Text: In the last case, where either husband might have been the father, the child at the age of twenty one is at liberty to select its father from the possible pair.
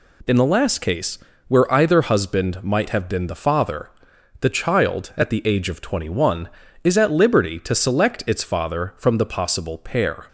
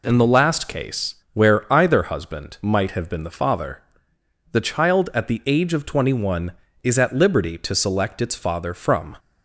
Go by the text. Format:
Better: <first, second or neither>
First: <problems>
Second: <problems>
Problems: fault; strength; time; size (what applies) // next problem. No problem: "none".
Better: first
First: none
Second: stops before "the possible pair"; at 9.1 s